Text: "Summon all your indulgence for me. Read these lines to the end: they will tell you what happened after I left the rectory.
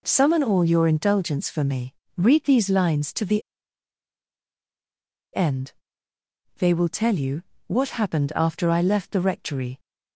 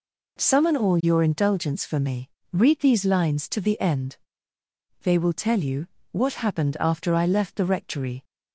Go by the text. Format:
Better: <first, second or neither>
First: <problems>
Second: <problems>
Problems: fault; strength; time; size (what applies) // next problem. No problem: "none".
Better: second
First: pauses between "the" and "end"; strong; at 3.4 s; 1.9 s long // pauses between "you" and "what"; slight; at 7.4 s; 0.26 s long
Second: pauses between "you" and "what"; slight; at 5.8 s; 0.26 s long